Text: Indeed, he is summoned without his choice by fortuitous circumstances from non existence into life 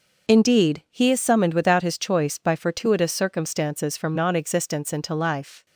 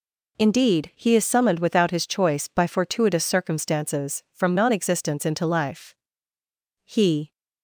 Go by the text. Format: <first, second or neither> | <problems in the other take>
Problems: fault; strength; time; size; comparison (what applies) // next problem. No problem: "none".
first | goes on to say "He"; slight; from 6.8 s on; 0.48 s long